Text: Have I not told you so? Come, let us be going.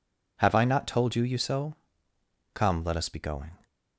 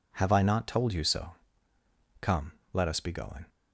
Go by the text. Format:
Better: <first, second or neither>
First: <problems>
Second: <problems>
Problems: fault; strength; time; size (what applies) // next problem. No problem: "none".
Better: second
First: says "you" twice; at 1.2 s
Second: none